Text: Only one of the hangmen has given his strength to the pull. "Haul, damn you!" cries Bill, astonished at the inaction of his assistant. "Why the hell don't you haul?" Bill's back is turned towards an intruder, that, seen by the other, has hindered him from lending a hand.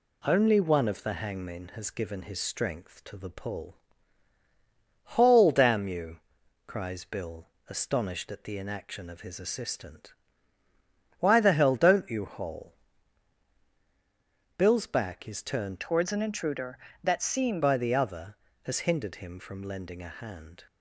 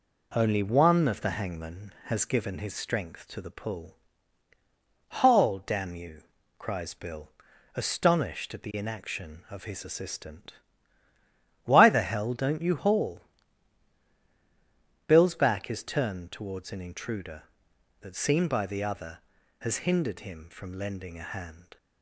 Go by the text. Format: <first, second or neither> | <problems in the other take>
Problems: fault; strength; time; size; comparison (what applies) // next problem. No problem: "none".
second | changes voice from "towards" to "seen"; from 15.8 to 17.6 s; 1.8 s long